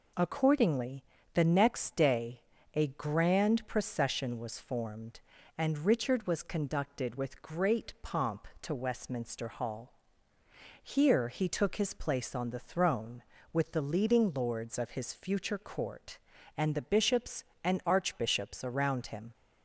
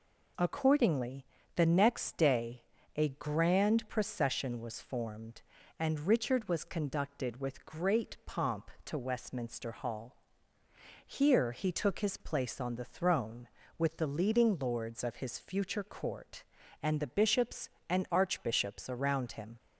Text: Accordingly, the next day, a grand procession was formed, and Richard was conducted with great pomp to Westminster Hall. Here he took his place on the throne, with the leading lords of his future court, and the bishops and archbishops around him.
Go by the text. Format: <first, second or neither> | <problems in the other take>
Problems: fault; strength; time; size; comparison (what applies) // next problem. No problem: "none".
neither | none